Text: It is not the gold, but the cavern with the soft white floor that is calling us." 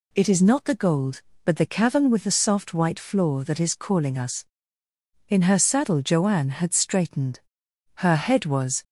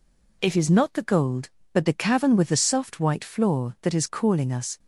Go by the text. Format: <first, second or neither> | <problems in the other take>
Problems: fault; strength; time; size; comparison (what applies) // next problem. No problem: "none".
second | goes on to say "In her saddle Joanne had straightened Her head was"; strong; from 5.2 s on; 3.5 s long